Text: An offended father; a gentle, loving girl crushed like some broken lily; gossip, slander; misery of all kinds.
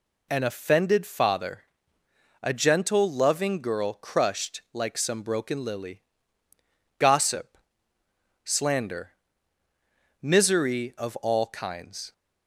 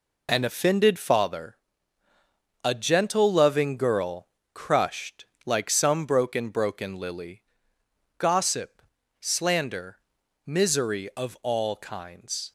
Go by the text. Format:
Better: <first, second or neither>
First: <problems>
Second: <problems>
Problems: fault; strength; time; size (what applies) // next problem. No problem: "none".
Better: first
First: none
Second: pauses between "girl" and "crushed"; slight; at 4.2 s; 0.26 s long // pauses between "crushed" and "like"; slight; at 5.2 s; 0.18 s long // says "broken" twice; at 6.4 s